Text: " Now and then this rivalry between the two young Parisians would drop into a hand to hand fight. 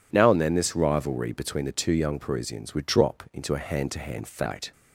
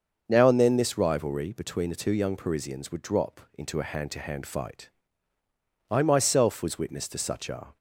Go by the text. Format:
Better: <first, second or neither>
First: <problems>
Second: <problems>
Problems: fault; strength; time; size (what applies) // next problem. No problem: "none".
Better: first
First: none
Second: starts louder than the rest; until 1.2 s; 6.5 dB // goes on to say "I myself was witness to such a"; strong; from 5.8 s on; 1.8 s long